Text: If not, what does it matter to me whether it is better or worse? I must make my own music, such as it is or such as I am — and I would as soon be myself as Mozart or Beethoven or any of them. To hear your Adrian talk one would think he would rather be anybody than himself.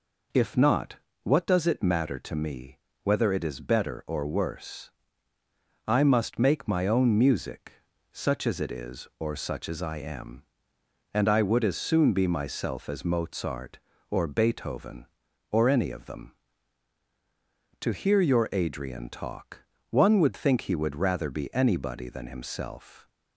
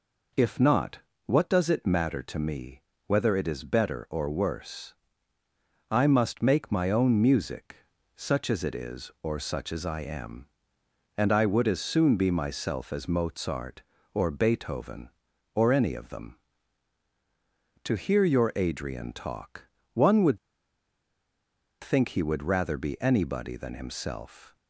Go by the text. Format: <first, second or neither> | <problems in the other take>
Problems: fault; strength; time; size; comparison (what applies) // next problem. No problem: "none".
first | pauses between "me" and "whether"; slight; at 2.8 s; 0.24 s long; slight in the first // pauses between "talk" and "one"; slight; at 19.6 s; 0.28 s long; slight in the first // pauses between "would" and "think"; strong; at 20.3 s; 1.4 s long